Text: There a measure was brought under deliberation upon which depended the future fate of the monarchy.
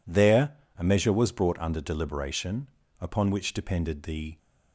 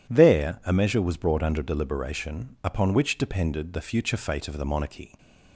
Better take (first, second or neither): second